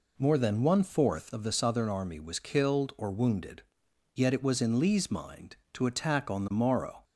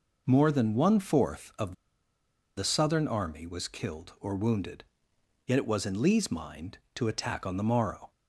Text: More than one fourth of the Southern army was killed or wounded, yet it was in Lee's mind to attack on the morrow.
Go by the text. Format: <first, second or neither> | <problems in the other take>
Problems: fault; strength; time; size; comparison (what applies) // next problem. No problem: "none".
first | pauses between "of" and "the"; noticeable; at 1.7 s; 0.83 s long